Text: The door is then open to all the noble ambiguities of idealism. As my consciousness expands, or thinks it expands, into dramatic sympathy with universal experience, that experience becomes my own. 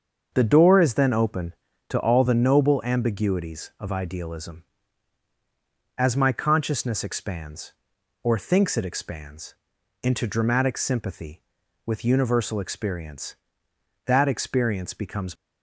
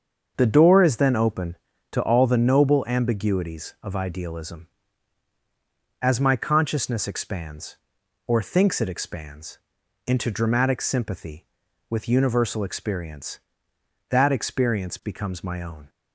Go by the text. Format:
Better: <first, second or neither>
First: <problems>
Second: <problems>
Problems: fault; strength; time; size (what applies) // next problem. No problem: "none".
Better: second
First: starts louder than the rest; until 1.3 s; 6.5 dB // stops before "my own"; at 15.3 s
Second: starts louder than the rest; until 1.3 s; 6.5 dB